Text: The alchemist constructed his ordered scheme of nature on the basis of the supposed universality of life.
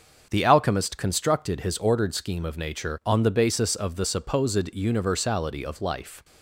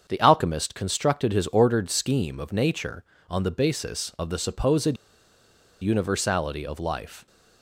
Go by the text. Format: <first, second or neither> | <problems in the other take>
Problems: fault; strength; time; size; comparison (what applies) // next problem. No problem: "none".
first | starts louder than the rest; until 1.0 s; 7 dB; also in the first // pauses between "supposed" and "universality"; noticeable; at 4.9 s; 0.85 s long